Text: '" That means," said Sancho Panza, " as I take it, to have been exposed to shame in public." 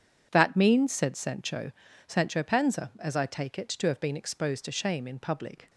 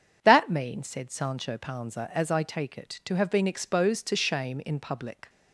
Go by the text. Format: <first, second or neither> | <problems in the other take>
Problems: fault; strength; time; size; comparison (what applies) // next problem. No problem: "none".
second | starts louder than the rest; strong; until 1.3 s; 8 dB // says "Sancho" twice; at 2.0 s